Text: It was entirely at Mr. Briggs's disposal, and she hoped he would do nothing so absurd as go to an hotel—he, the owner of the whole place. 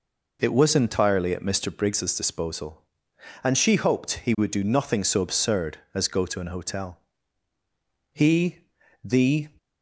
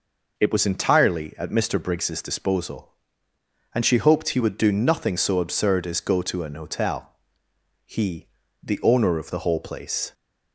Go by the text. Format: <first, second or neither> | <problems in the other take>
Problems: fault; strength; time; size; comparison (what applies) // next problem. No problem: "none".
second | stops before "owner of the whole place"; at 9.5 s